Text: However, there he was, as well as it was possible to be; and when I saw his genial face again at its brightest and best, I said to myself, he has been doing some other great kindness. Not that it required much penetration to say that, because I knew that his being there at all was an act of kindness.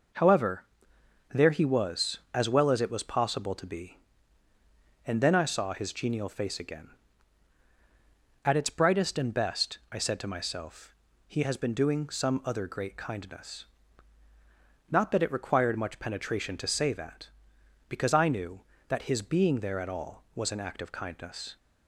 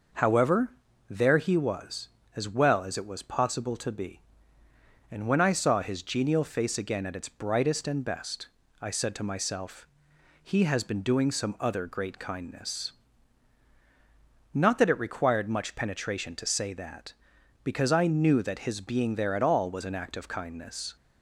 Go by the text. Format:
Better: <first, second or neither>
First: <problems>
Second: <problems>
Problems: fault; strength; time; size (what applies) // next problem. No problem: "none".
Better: second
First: says "then" for "when"; at 5.2 s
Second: none